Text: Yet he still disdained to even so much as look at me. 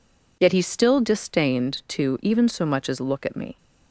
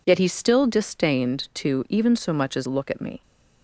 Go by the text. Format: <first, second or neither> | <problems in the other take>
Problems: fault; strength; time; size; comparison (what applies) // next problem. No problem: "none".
neither | none